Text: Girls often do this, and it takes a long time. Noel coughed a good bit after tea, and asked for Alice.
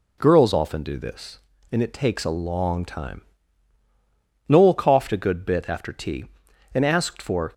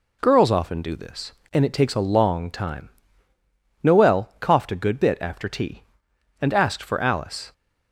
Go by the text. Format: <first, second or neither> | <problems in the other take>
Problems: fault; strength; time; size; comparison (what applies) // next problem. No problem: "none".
second | stops before "Alice"; at 7.5 s